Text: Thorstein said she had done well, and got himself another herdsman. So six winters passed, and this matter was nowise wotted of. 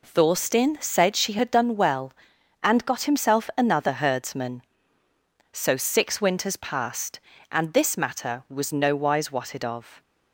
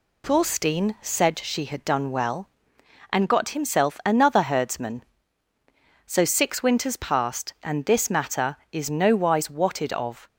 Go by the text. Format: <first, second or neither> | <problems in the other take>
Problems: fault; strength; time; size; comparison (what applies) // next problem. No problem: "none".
first | says "is" for "was"; at 8.7 s